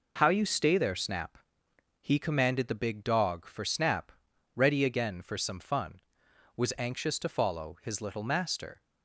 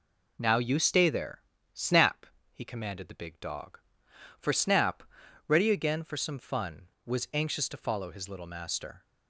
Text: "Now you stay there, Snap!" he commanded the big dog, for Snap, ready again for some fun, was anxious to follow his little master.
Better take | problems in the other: second | says "How" for "Now"; at 0.1 s

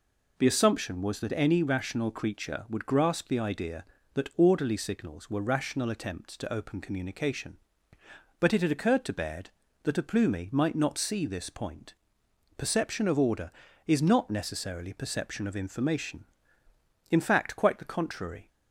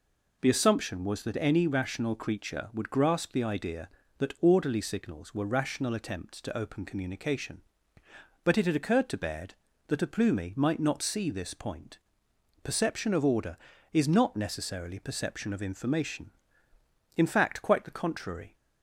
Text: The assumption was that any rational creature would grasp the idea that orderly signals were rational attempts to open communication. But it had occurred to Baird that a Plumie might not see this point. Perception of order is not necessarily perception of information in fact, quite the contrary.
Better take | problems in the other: neither | none

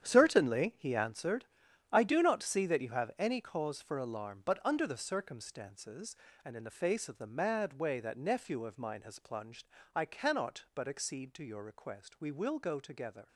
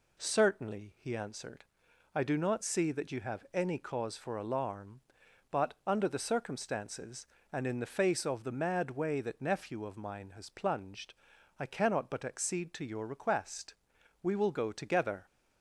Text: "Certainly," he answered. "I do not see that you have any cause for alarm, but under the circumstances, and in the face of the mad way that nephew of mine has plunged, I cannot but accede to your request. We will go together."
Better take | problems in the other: second | gets quieter; strong; throughout; 13.5 dB

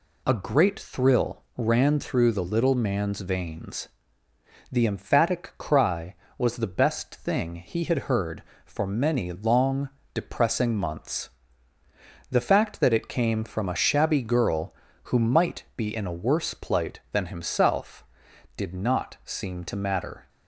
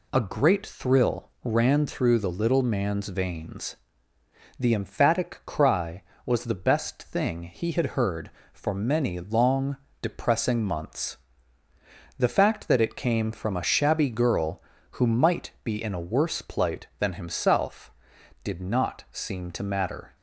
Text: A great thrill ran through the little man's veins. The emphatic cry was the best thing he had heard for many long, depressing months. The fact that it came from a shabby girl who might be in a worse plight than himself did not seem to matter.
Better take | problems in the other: neither | none

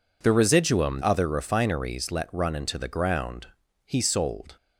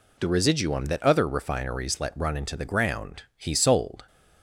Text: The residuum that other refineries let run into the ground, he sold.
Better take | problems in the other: second | skips "that"; at 1.0 s

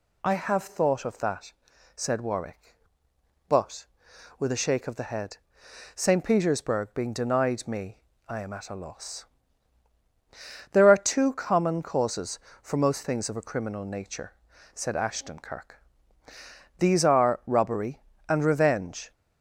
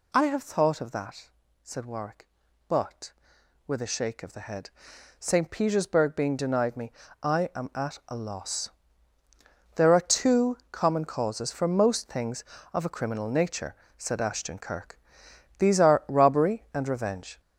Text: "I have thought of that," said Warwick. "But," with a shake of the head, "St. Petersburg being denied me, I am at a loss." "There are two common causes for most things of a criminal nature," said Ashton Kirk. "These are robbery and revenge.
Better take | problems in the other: first | gets louder; noticeable; throughout; 5.5 dB

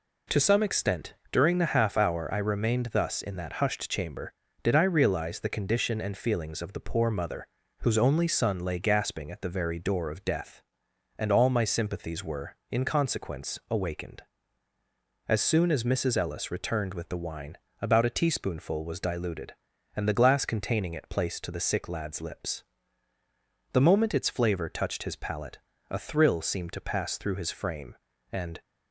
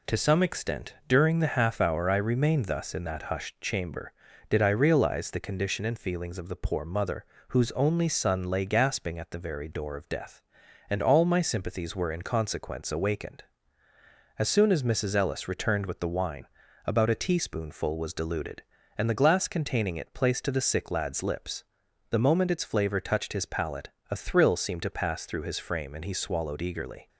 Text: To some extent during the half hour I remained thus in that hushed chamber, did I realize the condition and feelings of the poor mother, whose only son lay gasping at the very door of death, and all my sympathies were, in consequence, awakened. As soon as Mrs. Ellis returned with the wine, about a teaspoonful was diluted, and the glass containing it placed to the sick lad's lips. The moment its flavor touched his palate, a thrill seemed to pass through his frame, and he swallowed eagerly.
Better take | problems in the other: second | pauses between "extent" and "during"; slight; at 1.1 s; 0.16 s long // stops before "he swallowed eagerly"; at 28.6 s

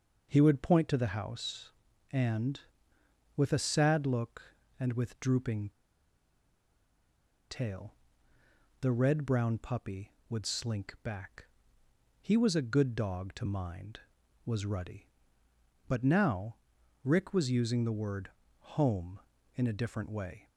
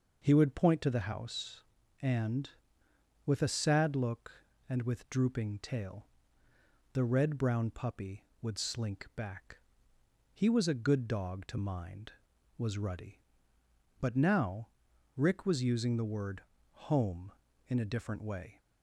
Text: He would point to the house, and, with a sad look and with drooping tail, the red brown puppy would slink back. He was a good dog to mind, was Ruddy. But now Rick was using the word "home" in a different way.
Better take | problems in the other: second | pauses between "drooping" and "tail"; strong; at 5.6 s; 1.8 s long // pauses between "now" and "Rick"; noticeable; at 16.5 s; 0.48 s long; noticeable in the second // pauses between "word" and "home"; slight; at 18.2 s; 0.32 s long; slight in the second

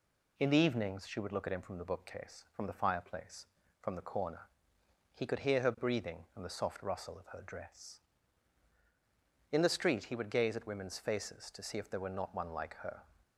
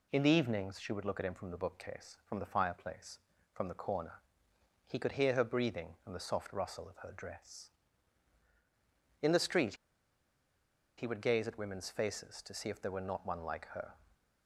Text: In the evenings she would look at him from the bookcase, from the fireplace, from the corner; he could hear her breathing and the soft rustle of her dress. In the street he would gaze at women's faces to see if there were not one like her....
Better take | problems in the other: first | pauses between "street" and "he"; at 9.7 s; 1.2 s long

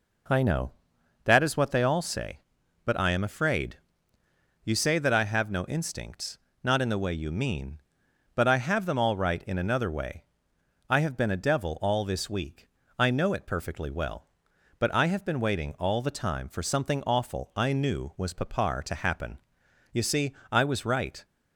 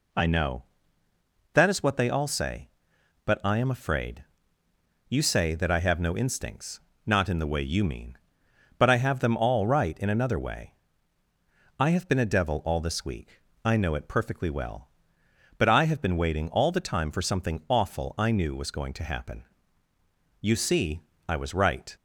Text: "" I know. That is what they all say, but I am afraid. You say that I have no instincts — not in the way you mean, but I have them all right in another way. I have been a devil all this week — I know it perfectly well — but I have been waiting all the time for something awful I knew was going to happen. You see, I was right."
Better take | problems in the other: second | says "papar" for "going"; at 18.3 s

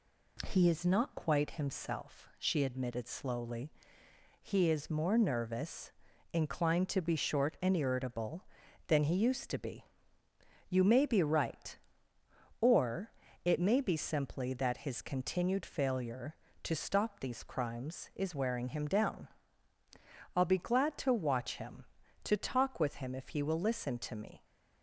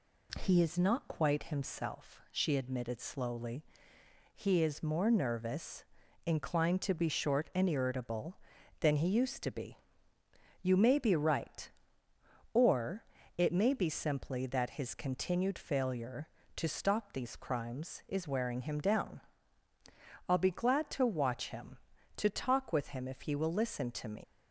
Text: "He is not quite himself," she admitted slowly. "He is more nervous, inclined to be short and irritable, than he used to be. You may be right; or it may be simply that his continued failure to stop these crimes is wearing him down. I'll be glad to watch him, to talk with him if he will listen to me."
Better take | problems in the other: first | pauses between "or" and "it"; slight; at 13.0 s; 0.34 s long; slight in the first // leaves "me" unfinished; at 24.2 s; 125 ms

